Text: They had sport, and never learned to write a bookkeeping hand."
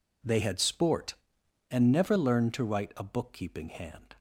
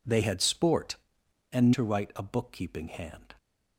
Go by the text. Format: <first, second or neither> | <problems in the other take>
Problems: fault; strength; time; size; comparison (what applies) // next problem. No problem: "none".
first | skips "never learned"; at 1.7 s